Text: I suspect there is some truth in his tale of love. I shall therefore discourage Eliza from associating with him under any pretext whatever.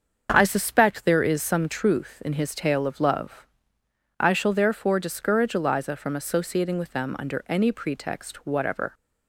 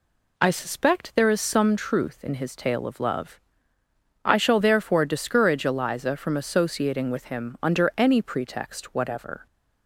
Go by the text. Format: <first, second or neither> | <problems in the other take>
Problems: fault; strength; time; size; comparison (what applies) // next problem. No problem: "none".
second | starts louder than the rest; until 1.3 s; 7 dB // says "them" for "him"; at 6.9 s